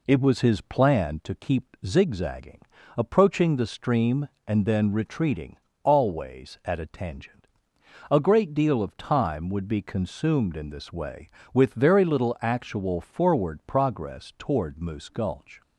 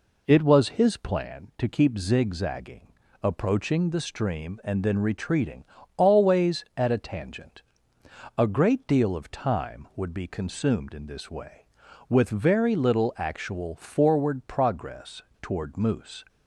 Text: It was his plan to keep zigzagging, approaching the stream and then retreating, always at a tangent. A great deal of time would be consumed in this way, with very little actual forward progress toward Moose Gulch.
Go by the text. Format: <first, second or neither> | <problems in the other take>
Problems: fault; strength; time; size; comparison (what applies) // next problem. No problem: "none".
first | pauses between "progress" and "toward"; slight; at 15.2 s; 0.19 s long // stops before "Gulch"; at 16.2 s